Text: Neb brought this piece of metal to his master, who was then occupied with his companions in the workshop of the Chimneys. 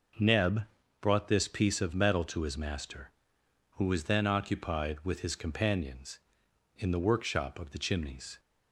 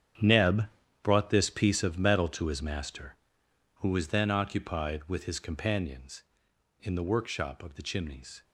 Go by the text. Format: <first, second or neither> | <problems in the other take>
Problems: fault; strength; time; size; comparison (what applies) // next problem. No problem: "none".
first | gets quieter; strong; throughout; 13 dB // pauses between "Neb" and "brought"; slight; at 0.6 s; 0.34 s long; slight in the first